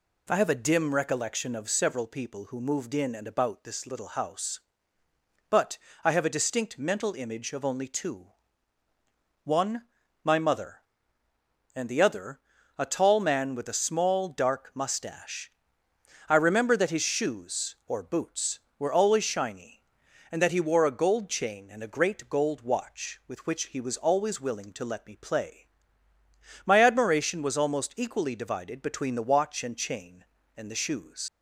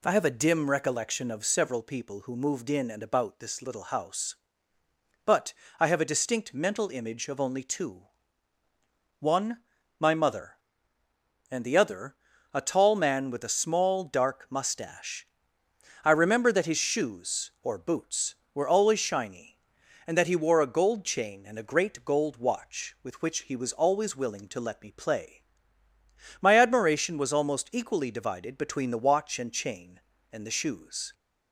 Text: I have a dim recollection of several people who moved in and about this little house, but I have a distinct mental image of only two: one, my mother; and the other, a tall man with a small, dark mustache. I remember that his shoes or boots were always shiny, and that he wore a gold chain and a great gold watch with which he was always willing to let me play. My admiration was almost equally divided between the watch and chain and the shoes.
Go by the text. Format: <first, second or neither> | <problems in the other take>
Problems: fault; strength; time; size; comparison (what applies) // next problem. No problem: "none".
second | pauses between "but" and "I"; slight; at 5.7 s; 0.26 s long; slight in the second // leaves "shoes" unfinished; at 31.2 s; 95 ms